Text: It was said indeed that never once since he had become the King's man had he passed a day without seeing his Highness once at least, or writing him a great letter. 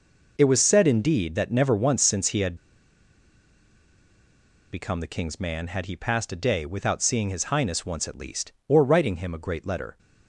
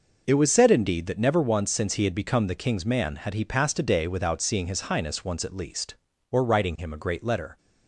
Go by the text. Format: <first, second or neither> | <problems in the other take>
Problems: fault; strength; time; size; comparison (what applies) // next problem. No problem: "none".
second | pauses between "had" and "become"; strong; at 2.5 s; 2.1 s long